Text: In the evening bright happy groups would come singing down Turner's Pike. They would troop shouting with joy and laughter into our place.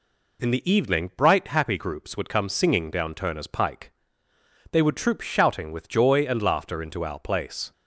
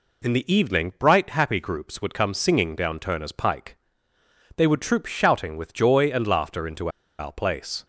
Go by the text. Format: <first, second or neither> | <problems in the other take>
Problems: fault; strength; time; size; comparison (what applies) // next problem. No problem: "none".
first | pauses between "into" and "our"; slight; at 6.8 s; 0.30 s long